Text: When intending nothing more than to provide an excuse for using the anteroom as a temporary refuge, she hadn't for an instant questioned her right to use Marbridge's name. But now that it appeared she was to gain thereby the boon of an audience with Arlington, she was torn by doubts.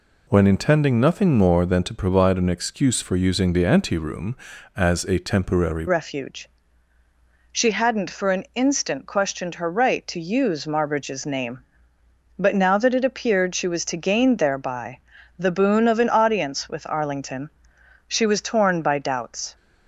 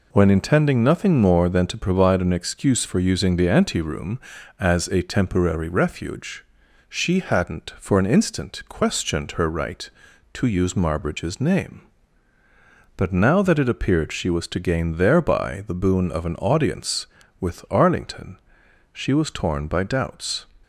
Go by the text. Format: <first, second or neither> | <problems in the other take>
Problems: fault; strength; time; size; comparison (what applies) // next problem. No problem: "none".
second | changes voice at "refuge"; from 5.8 s on; 13.7 s long // pauses between "thereby" and "the"; at 14.9 s; 0.40 s long